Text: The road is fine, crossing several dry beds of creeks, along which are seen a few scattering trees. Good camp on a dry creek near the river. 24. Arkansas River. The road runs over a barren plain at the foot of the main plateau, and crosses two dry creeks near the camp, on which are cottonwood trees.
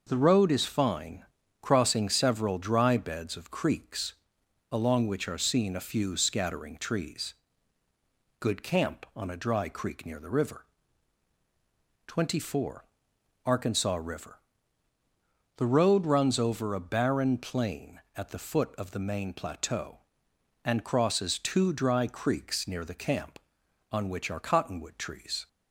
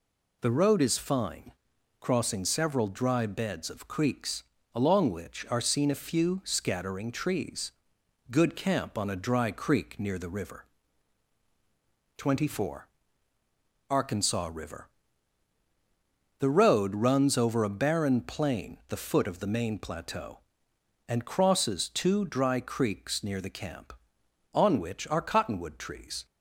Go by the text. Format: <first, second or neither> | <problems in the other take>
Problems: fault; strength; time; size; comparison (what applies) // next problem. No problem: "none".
first | skips "at"; at 18.8 s